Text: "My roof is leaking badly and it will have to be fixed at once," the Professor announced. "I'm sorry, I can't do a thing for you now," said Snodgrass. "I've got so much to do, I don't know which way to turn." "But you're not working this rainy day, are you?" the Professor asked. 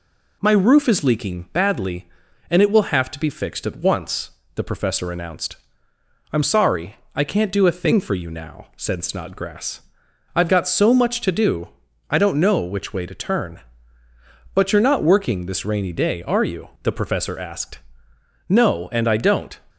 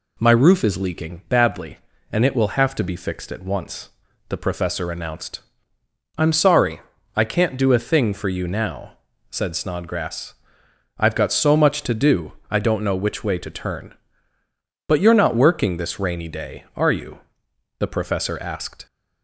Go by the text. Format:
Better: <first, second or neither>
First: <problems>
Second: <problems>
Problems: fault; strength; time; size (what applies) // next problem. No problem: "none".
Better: second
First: goes on to say "No and I don't"; noticeable; from 18.4 s on; 1.1 s long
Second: none